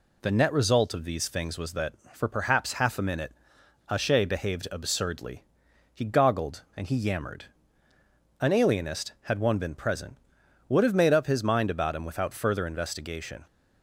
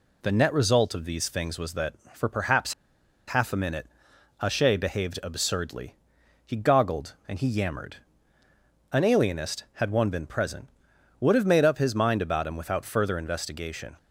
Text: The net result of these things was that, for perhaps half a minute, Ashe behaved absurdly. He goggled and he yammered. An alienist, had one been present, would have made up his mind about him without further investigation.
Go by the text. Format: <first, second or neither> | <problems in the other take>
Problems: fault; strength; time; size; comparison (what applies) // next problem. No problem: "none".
first | pauses between "perhaps" and "half"; noticeable; at 2.7 s; 0.54 s long